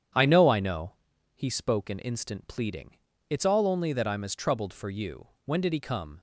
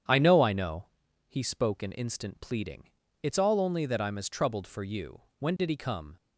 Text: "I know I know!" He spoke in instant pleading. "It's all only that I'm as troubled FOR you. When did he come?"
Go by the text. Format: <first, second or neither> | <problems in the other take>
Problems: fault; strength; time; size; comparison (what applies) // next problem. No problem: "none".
neither | starts louder than the rest; strong; the same in both